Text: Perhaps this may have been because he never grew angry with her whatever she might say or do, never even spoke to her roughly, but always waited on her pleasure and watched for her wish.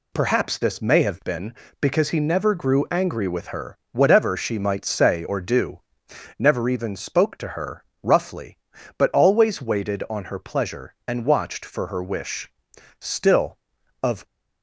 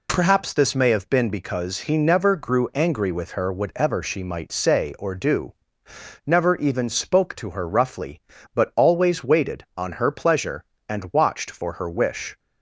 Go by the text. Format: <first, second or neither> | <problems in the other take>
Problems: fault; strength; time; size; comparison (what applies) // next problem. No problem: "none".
second | pauses between "her" and "roughly"; slight; at 7.8 s; 0.18 s long // goes on to say "Still of"; noticeable; from 12.9 s on; 1.2 s long